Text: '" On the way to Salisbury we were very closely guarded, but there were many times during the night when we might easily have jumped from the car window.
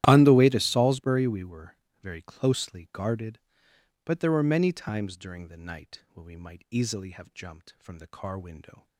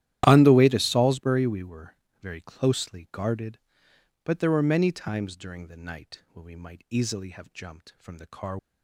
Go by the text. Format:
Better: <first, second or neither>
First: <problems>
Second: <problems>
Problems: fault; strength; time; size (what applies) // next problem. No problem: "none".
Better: first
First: starts louder than the rest; strong; until 1.0 s; 13 dB // pauses between "were" and "very"; slight; at 1.7 s; 0.26 s long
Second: starts louder than the rest; strong; until 1.2 s; 12.5 dB // pauses between "were" and "very"; slight; at 1.9 s; 0.26 s long // stops before "window"; at 8.5 s